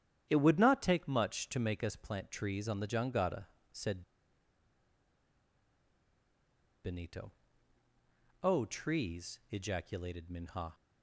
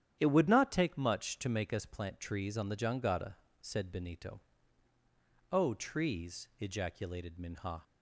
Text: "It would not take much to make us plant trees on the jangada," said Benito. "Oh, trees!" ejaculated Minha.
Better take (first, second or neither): second